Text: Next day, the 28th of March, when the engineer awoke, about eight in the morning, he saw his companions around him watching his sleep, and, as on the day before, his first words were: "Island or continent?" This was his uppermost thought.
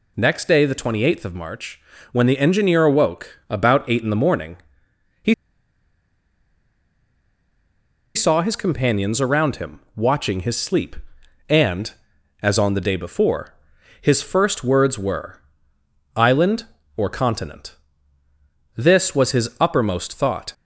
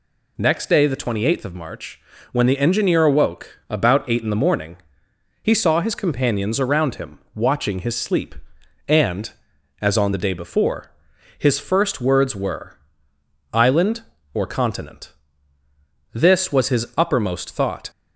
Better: second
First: pauses between "he" and "saw"; strong; at 5.3 s; 2.8 s long // pauses between "him" and "watching"; slight; at 9.7 s; 0.16 s long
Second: pauses between "him" and "watching"; slight; at 7.1 s; 0.16 s long

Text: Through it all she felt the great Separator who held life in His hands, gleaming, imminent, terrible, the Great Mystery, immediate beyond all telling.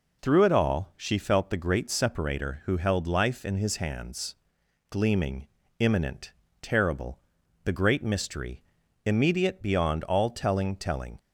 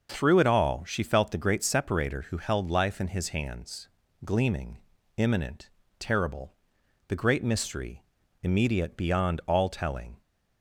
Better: second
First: says "telling" twice; at 10.7 s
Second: none

